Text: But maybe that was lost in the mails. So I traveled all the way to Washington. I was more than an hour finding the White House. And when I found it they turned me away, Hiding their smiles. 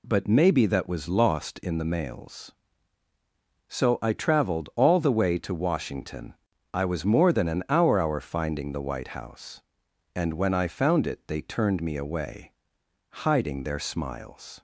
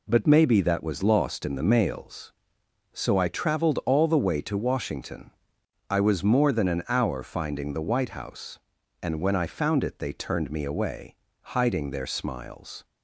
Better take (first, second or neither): second